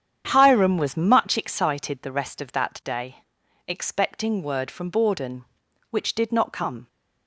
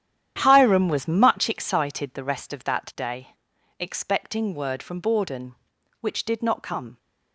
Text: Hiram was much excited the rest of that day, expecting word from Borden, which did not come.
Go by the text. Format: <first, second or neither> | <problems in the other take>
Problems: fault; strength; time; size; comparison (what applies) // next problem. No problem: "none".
first | gets quieter; strong; throughout; 11.5 dB // starts louder than the rest; strong; until 1.4 s; 10.5 dB; strong in the first